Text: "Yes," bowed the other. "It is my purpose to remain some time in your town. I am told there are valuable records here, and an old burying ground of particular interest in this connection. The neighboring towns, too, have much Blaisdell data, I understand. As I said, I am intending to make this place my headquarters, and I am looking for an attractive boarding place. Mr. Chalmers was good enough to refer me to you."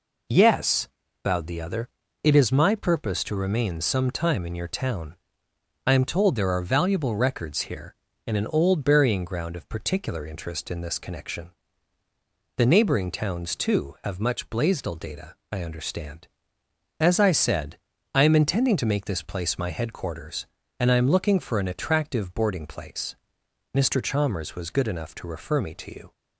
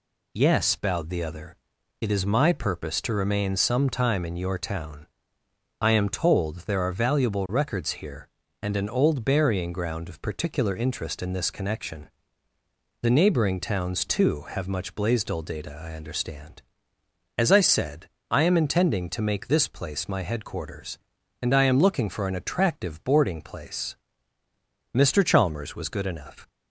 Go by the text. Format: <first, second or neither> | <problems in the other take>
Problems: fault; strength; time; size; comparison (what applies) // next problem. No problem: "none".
first | stops before "to refer me to you"; at 26.4 s